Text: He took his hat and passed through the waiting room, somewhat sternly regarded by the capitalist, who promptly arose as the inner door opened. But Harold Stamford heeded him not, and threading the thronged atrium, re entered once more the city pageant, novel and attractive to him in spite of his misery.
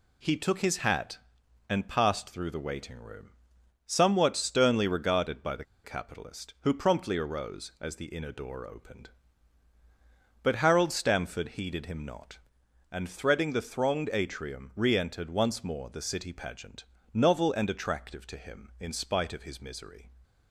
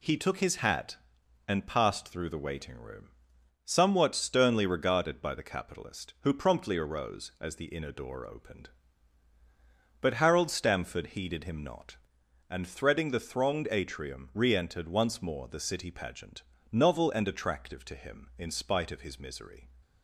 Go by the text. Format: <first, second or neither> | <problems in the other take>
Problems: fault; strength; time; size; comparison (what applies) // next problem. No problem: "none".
second | pauses between "the" and "capitalist"; slight; at 5.6 s; 0.20 s long